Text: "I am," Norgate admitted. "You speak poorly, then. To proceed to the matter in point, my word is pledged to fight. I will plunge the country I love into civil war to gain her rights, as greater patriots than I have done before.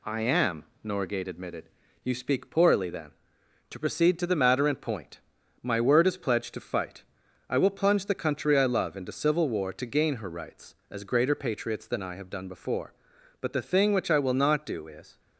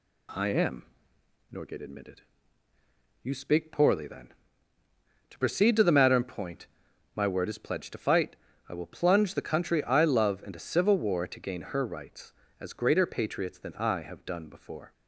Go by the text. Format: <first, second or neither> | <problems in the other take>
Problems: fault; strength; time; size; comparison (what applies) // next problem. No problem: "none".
second | goes on to say "But the thing which I will not do is"; strong; from 13.3 s on; 1.8 s long